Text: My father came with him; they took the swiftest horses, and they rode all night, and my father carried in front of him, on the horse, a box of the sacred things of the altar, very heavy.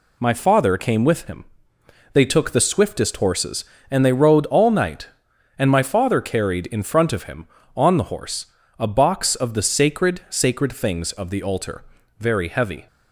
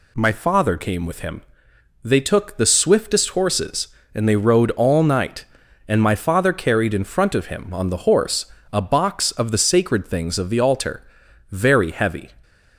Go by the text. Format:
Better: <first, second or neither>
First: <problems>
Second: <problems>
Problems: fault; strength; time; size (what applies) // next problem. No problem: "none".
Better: second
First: says "sacred" twice; at 10.2 s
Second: none